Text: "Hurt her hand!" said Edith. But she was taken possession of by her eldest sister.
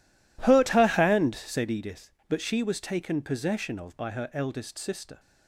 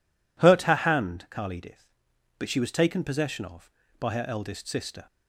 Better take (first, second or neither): first